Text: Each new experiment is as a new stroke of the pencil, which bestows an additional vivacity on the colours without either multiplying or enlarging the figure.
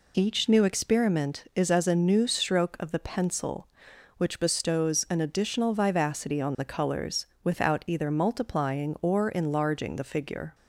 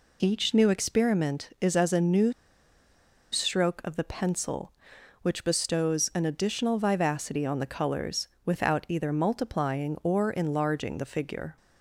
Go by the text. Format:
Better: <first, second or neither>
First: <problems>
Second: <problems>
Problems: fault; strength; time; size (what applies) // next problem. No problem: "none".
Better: first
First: pauses between "colours" and "without"; slight; at 7.2 s; 0.20 s long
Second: pauses between "new" and "stroke"; at 2.3 s; 1.0 s long // pauses between "colours" and "without"; slight; at 8.2 s; 0.20 s long